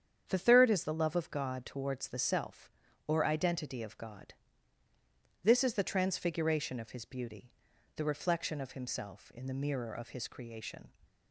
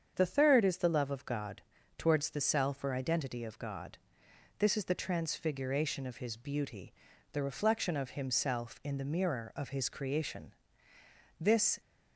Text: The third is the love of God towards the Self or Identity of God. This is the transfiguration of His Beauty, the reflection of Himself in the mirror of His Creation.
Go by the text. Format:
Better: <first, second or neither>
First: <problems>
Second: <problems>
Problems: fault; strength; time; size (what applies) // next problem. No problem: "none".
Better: first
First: starts louder than the rest; strong; until 1.2 s; 8 dB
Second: starts louder than the rest; strong; until 1.1 s; 7.5 dB // pauses between "God" and "towards"; at 1.6 s; 0.38 s long // goes on to say "This"; slight; from 11.4 s on; 0.40 s long